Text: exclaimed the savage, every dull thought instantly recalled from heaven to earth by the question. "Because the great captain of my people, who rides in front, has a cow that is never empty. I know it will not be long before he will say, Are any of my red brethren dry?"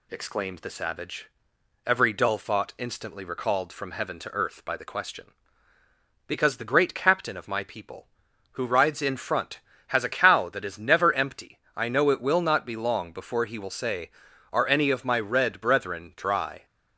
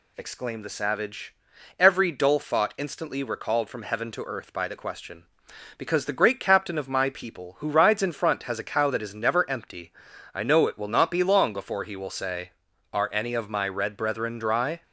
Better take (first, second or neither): neither